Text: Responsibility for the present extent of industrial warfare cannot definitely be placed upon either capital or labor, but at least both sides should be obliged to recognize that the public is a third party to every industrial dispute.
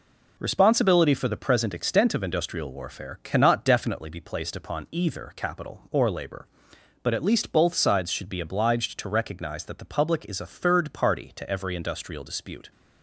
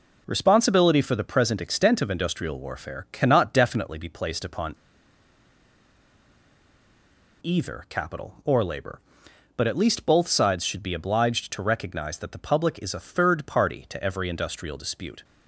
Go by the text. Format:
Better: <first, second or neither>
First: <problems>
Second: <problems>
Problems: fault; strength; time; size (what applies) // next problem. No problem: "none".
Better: first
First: none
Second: pauses between "upon" and "either"; strong; at 4.7 s; 2.6 s long